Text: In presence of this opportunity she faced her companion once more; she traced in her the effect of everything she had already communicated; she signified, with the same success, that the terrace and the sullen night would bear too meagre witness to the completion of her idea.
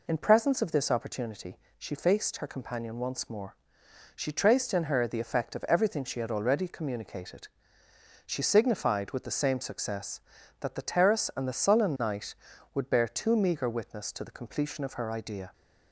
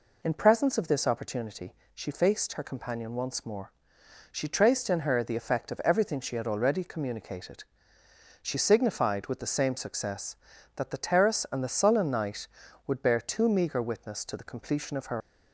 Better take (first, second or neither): first